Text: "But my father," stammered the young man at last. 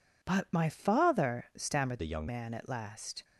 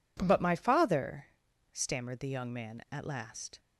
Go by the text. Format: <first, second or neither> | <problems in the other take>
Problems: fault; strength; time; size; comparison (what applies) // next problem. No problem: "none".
second | changes voice from "the" to "young"; from 1.9 to 2.2 s; 0.3 s long